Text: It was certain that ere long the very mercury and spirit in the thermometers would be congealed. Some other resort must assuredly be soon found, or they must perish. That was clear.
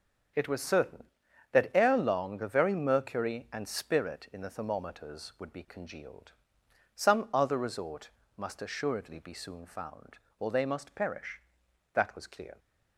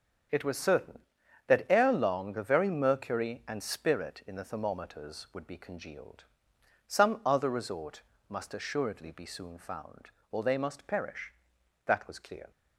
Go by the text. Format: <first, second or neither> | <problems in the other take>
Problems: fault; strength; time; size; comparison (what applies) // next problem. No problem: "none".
neither | starts louder than the rest; the same in both // pauses between "resort" and "must"; slight; the same in both